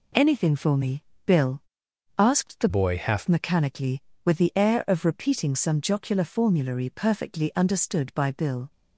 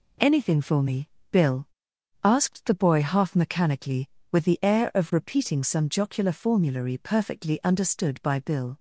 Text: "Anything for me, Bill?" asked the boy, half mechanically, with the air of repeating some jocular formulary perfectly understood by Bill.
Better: second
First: changes voice from "boy" to "half"; from 2.6 to 3.2 s; 0.6 s long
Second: none

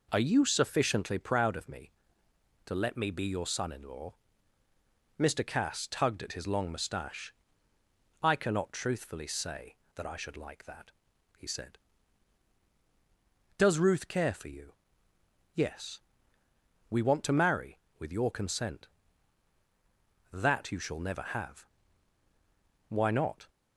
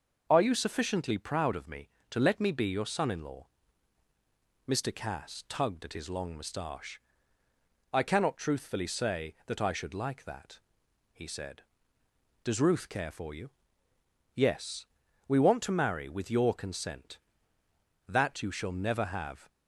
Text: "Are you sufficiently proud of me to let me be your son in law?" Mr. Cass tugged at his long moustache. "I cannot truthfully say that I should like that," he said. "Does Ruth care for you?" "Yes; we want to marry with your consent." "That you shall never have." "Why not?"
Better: first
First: none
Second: starts louder than the rest; noticeable; until 1.3 s; 6 dB // stops before "Why not"; at 19.4 s

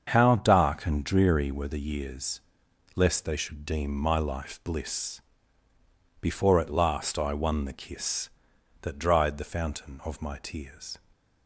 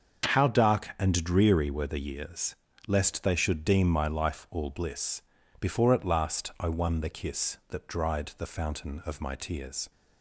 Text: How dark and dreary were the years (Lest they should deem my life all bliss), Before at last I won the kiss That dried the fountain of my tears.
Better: second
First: starts louder than the rest; until 1.1 s; 7 dB // skips "all"; at 4.6 s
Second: starts louder than the rest; until 1.3 s; 6.5 dB

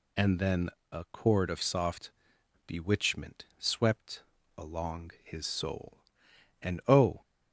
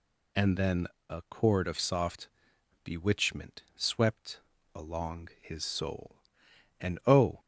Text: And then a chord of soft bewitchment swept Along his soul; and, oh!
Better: neither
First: pauses between "then" and "a"; slight; at 0.6 s; 0.22 s long // pauses between "soft" and "bewitchment"; noticeable; at 2.1 s; 0.56 s long // pauses between "swept" and "Along"; slight; at 4.2 s; 0.36 s long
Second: pauses between "then" and "a"; slight; at 0.8 s; 0.22 s long // pauses between "soft" and "bewitchment"; noticeable; at 2.2 s; 0.56 s long // pauses between "swept" and "Along"; slight; at 4.3 s; 0.36 s long

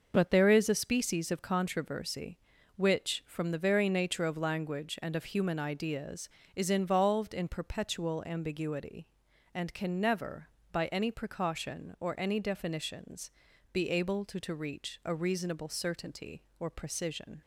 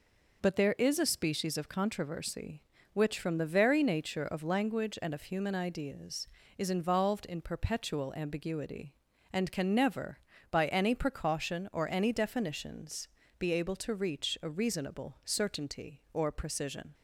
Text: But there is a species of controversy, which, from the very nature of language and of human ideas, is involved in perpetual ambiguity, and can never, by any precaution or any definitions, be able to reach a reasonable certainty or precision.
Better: second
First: says "to" twice; at 14.3 s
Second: none

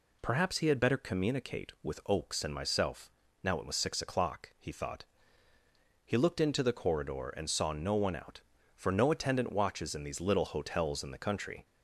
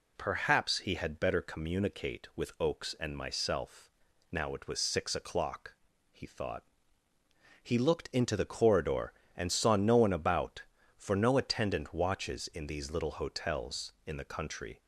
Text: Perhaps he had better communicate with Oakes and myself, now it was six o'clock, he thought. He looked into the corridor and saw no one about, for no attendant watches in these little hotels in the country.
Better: second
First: says "out" for "about"; at 8.1 s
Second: none

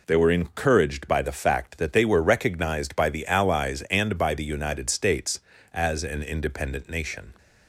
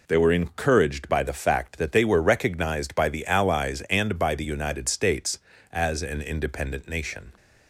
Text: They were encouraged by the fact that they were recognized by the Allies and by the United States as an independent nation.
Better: neither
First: none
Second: none

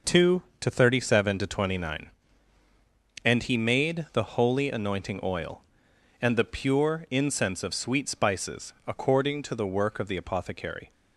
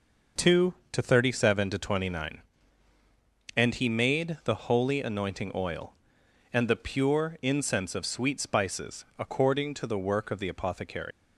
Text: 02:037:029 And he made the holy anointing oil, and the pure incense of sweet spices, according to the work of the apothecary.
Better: first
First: none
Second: leaves "apothecary" unfinished; at 11.1 s; 120 ms

